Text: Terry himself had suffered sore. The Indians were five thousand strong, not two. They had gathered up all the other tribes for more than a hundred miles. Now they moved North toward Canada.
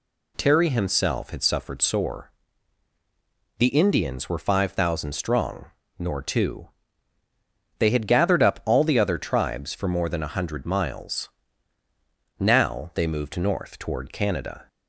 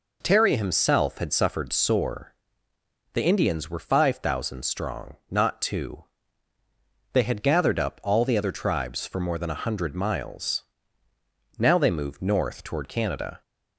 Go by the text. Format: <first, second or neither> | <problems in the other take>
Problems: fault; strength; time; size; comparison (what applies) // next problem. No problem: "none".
second | says "nor" for "not"; at 5.9 s